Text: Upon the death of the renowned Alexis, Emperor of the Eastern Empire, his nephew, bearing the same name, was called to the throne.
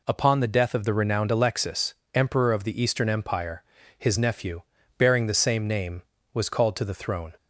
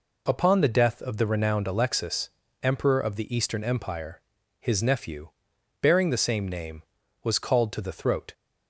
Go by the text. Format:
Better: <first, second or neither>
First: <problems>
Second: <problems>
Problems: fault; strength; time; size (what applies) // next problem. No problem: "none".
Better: first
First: none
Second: says "throat" for "throne"; at 7.9 s